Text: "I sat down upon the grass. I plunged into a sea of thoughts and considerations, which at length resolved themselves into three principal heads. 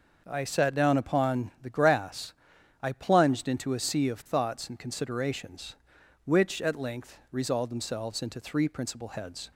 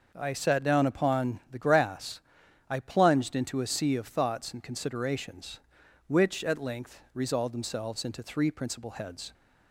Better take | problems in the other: neither | none

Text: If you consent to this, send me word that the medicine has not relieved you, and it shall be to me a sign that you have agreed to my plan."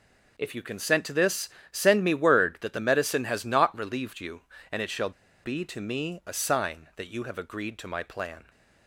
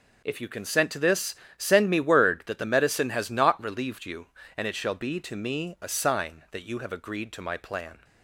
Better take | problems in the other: second | pauses between "shall" and "be"; slight; at 5.1 s; 0.33 s long

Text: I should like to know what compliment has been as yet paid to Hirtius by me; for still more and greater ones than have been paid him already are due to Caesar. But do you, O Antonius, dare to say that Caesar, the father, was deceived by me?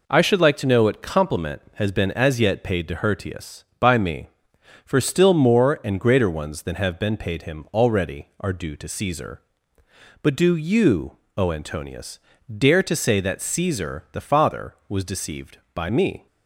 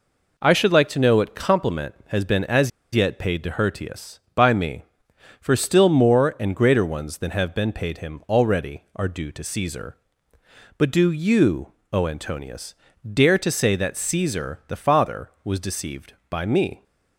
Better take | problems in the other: first | pauses between "as" and "yet"; slight; at 2.7 s; 0.23 s long

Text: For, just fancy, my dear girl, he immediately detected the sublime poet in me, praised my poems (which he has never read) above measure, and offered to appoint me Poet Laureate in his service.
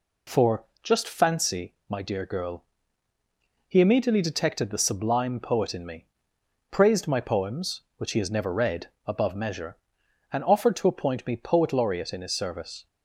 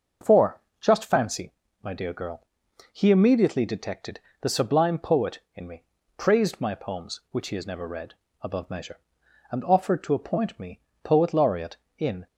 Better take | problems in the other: first | starts louder than the rest; until 1.4 s; 6.5 dB // pauses between "detected" and "the"; slight; at 4.1 s; 0.22 s long // pauses between "me" and "Poet"; slight; at 10.7 s; 0.22 s long // stops before "his service"; at 12.2 s

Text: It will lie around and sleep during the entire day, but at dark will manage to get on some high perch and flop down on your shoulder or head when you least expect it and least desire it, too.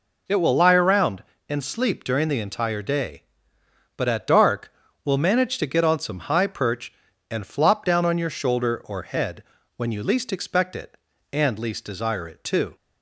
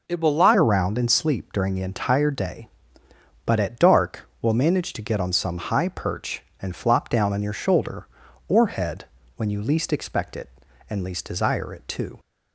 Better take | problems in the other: first | changes voice at "around"; from 0.5 s on; 11.6 s long // pauses between "head" and "when"; slight; at 9.0 s; 0.30 s long; slight in the first

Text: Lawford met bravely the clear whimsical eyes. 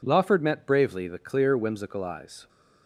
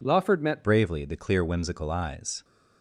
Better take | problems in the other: first | changes voice at "bravely"; from 0.6 s on; 1.8 s long

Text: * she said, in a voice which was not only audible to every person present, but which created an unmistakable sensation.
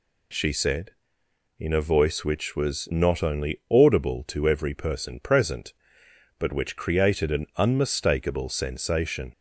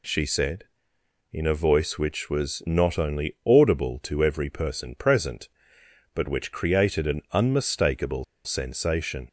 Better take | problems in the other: first | pauses between "unmistakable" and "sensation"; slight; at 8.2 s; 0.21 s long

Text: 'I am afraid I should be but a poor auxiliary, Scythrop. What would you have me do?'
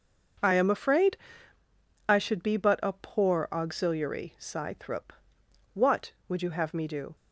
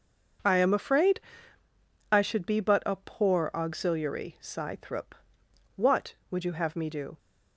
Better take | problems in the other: neither | pauses between "afraid" and "I"; noticeable; the same in both

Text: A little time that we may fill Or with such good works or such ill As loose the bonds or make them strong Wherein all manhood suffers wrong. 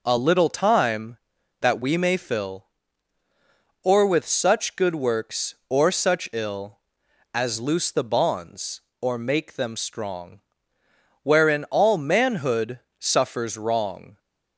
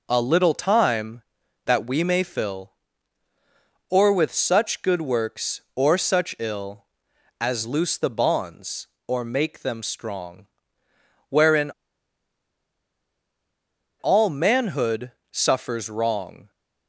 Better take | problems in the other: first | pauses between "strong" and "Wherein"; noticeable; at 10.4 s; 0.86 s long; noticeable in the first // pauses between "Wherein" and "all"; strong; at 11.7 s; 2.2 s long // pauses between "manhood" and "suffers"; slight; at 15.1 s; 0.22 s long; slight in the first

